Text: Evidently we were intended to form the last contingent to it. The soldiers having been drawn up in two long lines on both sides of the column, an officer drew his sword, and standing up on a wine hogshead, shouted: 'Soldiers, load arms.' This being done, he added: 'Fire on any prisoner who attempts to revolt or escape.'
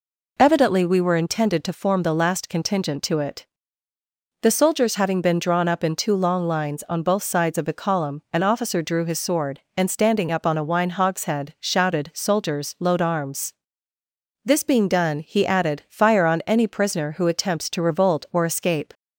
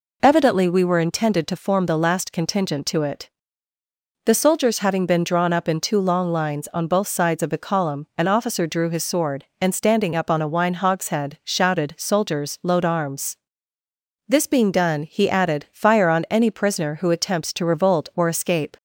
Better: neither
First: none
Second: none

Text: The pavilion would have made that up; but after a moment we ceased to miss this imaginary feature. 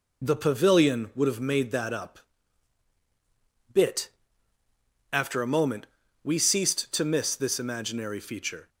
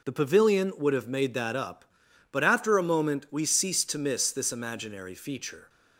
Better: second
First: says "bit" for "but"; at 3.7 s // pauses between "moment" and "we"; at 5.8 s; 0.38 s long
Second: none

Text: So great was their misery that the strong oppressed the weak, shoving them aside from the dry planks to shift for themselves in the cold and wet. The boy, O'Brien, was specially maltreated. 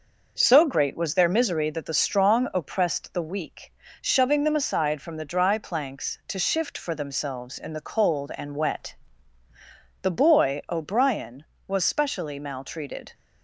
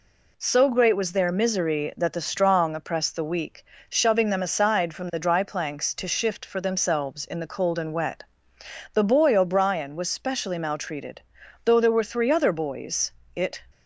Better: first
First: none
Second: goes on to say "Though there were three other boys it"; strong; from 11.6 s on; 1.9 s long

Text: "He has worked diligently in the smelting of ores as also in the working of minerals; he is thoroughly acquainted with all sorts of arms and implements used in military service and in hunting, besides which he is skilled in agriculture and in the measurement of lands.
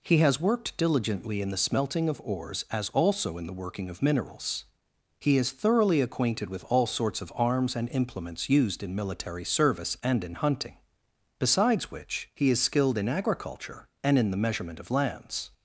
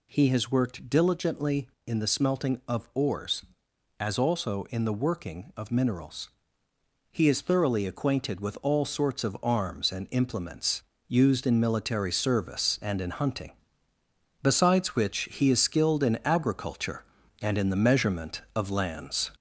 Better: first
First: none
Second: gets louder; noticeable; throughout; 4 dB // pauses between "implements" and "used"; slight; at 10.8 s; 0.26 s long

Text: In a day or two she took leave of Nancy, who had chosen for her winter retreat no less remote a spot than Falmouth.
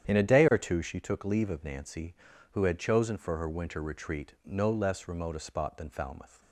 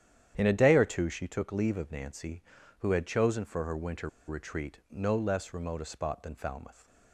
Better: first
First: starts louder than the rest; strong; until 1.1 s; 9.5 dB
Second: starts louder than the rest; strong; until 1.3 s; 10 dB // pauses between "winter" and "retreat"; slight; at 4.0 s; 0.18 s long

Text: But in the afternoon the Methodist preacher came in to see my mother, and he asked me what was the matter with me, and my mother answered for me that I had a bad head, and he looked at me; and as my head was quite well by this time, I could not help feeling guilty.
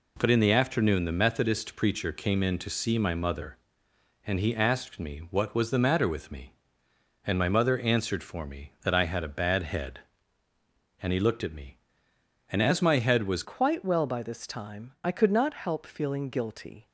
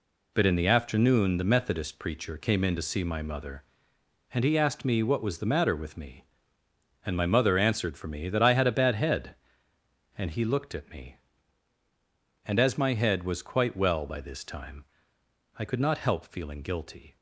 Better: second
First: changes voice at "quite"; from 13.4 s on; 3.4 s long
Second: none

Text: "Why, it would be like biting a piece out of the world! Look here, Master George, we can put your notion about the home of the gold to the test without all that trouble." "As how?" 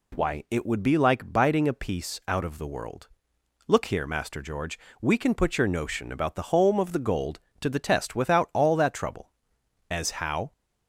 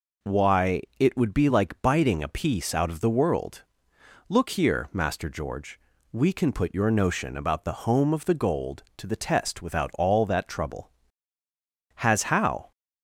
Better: first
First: none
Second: says "Has" for "As"; at 11.9 s

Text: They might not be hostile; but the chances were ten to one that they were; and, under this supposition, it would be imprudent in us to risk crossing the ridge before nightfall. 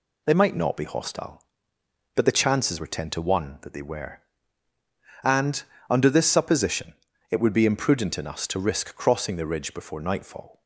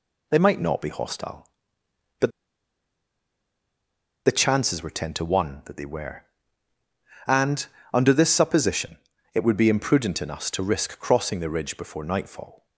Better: first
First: none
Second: pauses between "but" and "the"; strong; at 2.2 s; 1.9 s long

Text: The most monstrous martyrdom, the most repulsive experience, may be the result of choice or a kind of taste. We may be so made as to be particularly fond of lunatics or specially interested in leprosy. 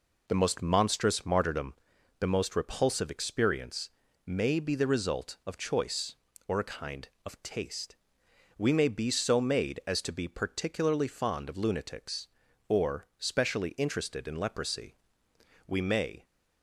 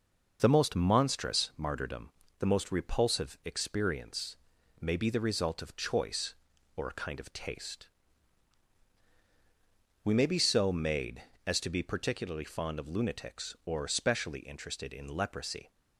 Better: second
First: goes on to say "We may"; from 15.6 s on; 0.58 s long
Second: none

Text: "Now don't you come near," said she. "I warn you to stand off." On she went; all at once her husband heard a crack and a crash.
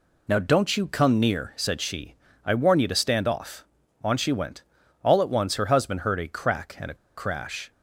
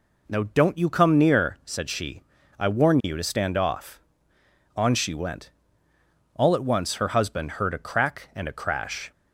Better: second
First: pauses between "a" and "crash"; slight; at 6.9 s; 0.22 s long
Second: none

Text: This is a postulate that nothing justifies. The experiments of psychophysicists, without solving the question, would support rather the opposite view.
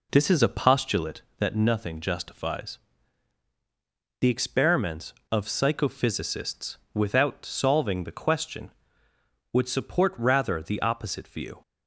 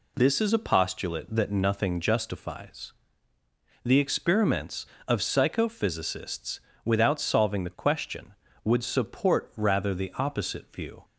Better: second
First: starts louder than the rest; until 1.2 s; 3.5 dB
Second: none

